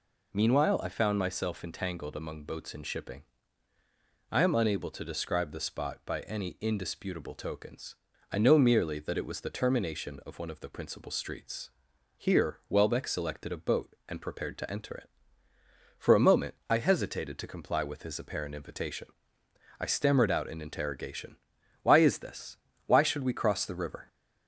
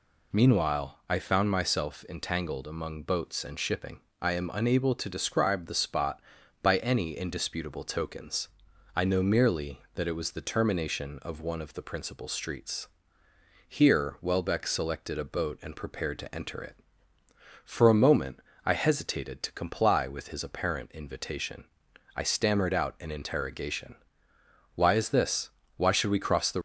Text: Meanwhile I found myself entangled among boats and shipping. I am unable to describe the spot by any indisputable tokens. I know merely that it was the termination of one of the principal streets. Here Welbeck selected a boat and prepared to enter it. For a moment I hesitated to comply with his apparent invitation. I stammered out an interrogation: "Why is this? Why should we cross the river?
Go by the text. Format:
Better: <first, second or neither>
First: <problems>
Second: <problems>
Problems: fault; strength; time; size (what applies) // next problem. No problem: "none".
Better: first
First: none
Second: pauses between "moment" and "I"; slight; at 18.3 s; 0.26 s long // stops before "river"; at 26.5 s